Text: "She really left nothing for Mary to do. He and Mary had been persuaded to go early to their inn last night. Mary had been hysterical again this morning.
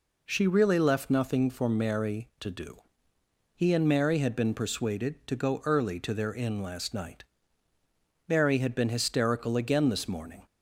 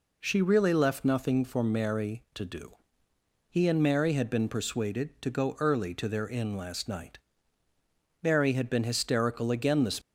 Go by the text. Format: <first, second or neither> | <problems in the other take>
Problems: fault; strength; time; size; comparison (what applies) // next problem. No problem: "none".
first | stops before "morning"; at 10.0 s